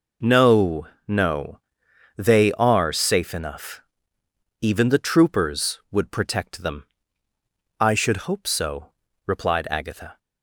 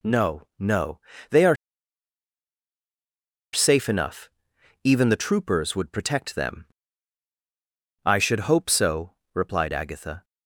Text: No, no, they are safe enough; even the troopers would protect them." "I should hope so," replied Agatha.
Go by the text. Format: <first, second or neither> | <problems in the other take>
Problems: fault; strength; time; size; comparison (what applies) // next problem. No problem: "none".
first | pauses between "are" and "safe"; strong; at 1.5 s; 1.9 s long